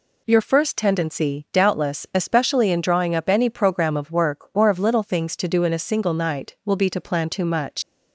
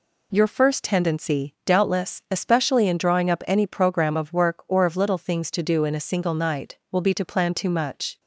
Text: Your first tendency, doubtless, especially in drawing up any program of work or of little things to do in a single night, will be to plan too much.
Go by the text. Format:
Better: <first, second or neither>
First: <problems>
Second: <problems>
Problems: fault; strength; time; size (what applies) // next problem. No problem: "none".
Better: second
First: leaves "much" unfinished; at 7.8 s; 110 ms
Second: none